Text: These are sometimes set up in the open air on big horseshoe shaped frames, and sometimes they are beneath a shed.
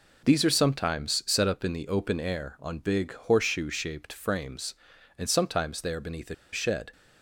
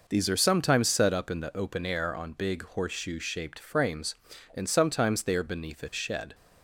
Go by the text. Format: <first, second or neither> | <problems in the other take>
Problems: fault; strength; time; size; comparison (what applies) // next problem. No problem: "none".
second | pauses between "a" and "shed"; slight; at 6.3 s; 0.18 s long